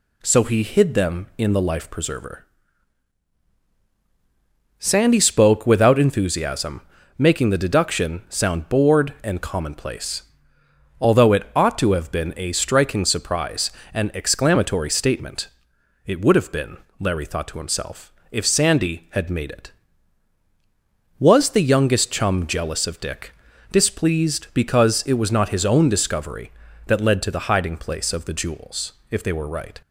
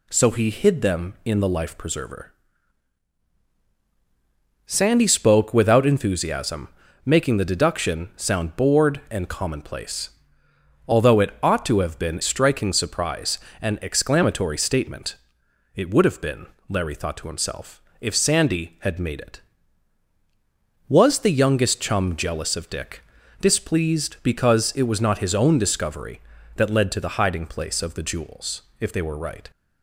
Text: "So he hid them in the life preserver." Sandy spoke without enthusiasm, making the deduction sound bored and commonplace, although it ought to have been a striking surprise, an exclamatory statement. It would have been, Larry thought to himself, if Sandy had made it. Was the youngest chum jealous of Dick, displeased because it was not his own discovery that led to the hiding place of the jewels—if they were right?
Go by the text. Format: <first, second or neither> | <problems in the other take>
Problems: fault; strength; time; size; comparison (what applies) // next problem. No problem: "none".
first | skips "a"; at 12.2 s